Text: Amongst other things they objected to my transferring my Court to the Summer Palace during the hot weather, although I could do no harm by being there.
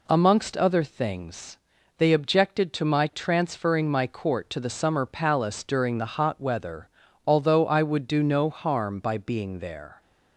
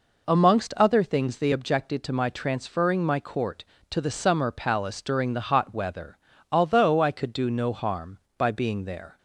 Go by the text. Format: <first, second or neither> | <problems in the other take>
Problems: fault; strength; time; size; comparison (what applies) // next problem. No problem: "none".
second | pauses between "things" and "they"; at 1.5 s; 0.40 s long // says "would" for "could"; at 7.8 s